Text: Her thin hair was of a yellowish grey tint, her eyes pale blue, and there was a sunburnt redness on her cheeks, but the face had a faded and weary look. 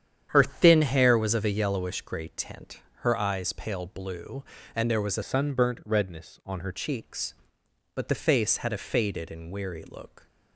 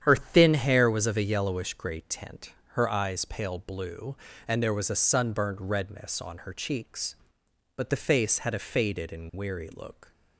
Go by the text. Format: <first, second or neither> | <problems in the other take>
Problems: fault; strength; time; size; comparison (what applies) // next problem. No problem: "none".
second | starts louder than the rest; strong; until 1.3 s; 9 dB; strong in the second // changes voice from "sunburnt" to "her"; from 5.2 to 6.7 s; 1.5 s long